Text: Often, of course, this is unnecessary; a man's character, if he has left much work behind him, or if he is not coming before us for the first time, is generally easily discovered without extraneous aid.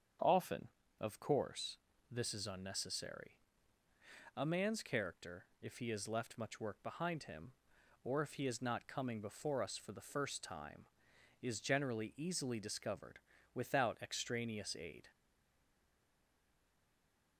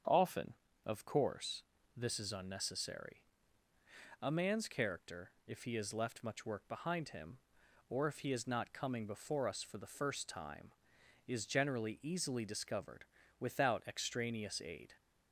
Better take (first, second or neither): second